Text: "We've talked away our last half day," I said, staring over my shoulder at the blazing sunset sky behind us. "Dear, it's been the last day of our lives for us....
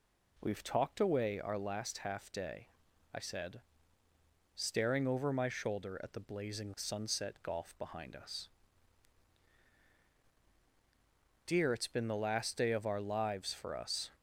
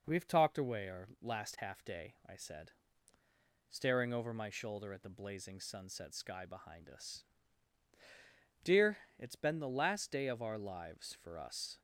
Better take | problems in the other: second | says "golf" for "sky"; at 7.4 s

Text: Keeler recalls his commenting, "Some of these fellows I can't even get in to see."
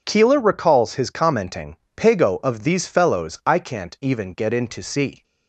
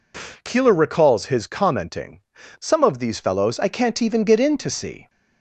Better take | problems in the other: second | says "Pago" for "Some"; at 1.9 s

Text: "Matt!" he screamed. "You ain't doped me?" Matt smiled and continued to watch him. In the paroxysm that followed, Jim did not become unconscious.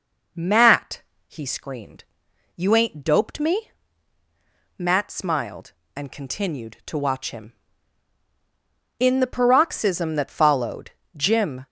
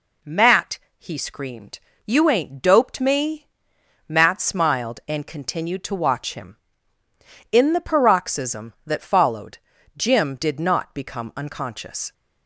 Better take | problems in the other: second | stops before "did not become unconscious"; at 11.6 s

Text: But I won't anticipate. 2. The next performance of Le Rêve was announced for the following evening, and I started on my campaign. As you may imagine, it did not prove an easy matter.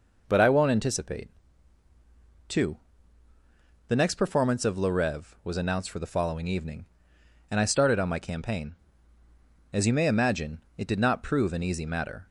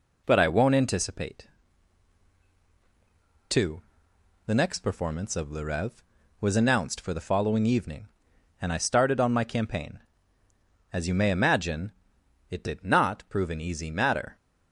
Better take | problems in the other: neither | none

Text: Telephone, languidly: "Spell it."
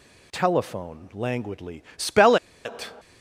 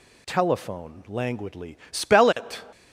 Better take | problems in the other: second | pauses between "Spell" and "it"; slight; at 2.3 s; 0.28 s long

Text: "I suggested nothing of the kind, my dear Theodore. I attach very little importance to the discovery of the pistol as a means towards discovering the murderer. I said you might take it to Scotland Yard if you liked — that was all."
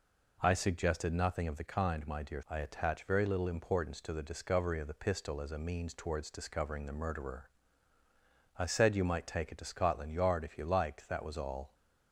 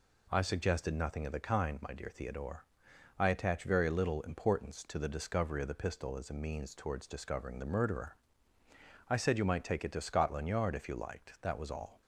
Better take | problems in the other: second | skips "Theodore"; at 2.4 s

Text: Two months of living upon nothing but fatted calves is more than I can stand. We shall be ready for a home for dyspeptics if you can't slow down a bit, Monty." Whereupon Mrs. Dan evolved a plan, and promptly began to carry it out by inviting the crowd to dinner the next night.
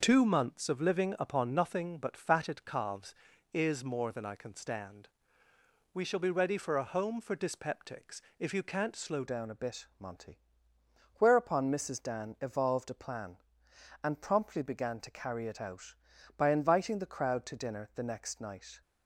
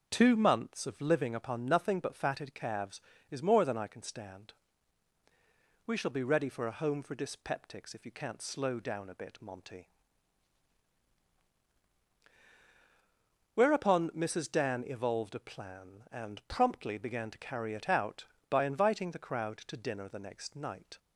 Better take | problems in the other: second | pauses between "dyspeptics" and "if"; slight; at 8.1 s; 0.20 s long // changes voice at "down"; from 9.2 s on; 9.6 s long

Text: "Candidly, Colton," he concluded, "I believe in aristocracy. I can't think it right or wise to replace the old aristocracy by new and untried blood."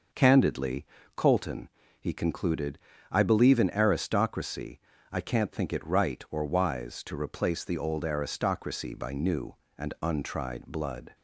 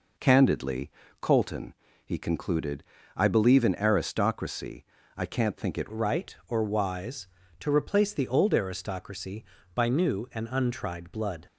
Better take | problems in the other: first | changes voice at "right"; from 5.9 s on; 5.5 s long

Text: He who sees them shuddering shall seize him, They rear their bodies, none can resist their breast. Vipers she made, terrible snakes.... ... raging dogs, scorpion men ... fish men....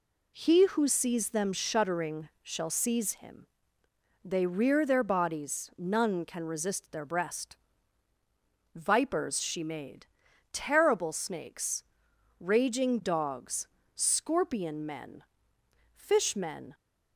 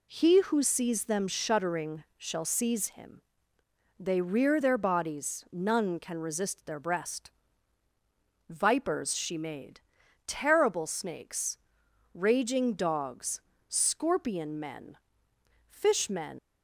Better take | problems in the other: first | leaves "men" unfinished; at 16.3 s; 85 ms

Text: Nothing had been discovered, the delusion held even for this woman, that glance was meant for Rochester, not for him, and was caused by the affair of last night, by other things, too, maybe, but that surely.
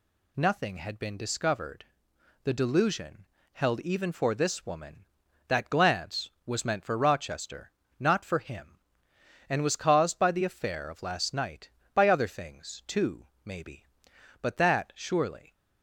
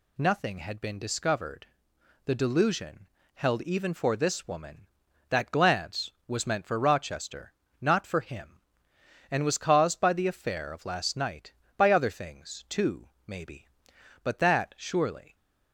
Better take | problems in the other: neither | pauses between "delusion" and "held"; slight; the same in both

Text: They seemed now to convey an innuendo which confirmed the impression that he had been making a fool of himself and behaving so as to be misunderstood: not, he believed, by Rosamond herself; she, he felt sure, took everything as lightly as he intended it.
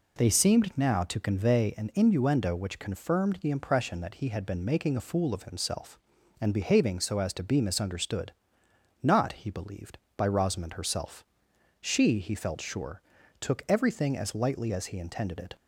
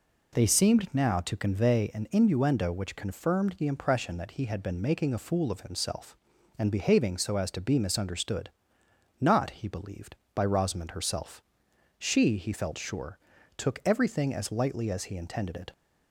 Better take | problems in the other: neither | none

